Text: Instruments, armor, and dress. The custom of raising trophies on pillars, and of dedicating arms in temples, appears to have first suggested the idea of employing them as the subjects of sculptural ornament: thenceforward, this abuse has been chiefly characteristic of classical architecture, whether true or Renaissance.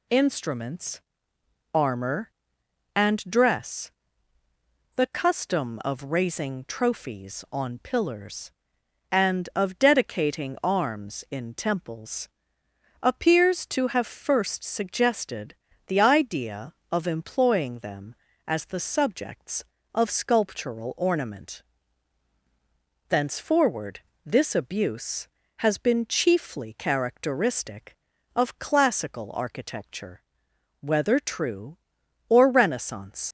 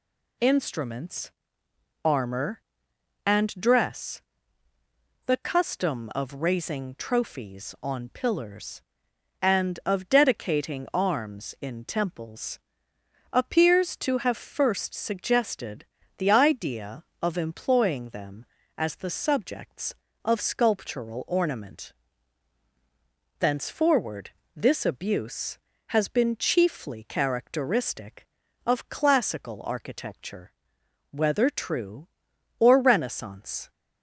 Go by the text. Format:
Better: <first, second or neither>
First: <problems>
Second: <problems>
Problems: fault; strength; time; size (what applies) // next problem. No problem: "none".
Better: second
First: pauses between "suggested" and "the"; slight; at 15.5 s; 0.32 s long // leaves "Renaissance" unfinished; at 33.2 s; 85 ms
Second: pauses between "suggested" and "the"; slight; at 15.8 s; 0.32 s long